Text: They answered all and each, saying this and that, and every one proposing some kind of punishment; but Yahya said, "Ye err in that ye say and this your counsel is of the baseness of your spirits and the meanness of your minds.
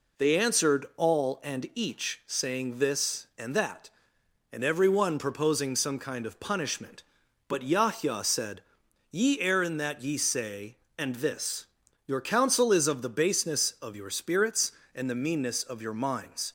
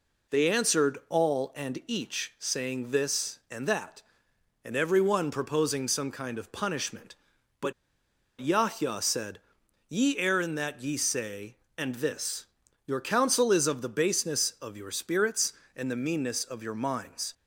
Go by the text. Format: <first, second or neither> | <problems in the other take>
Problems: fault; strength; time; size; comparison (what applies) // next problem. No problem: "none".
first | pauses between "but" and "Yahya"; noticeable; at 7.7 s; 0.68 s long // pauses between "this" and "your"; at 12.4 s; 0.40 s long; also in the first